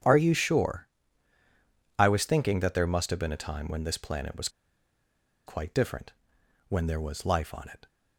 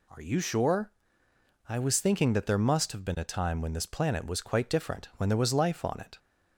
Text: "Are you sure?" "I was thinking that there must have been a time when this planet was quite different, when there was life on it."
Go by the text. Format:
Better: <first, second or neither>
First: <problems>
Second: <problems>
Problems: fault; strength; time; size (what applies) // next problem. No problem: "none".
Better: second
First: starts louder than the rest; strong; until 2.1 s; 9 dB // pauses between "was" and "quite"; noticeable; at 4.4 s; 0.97 s long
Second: none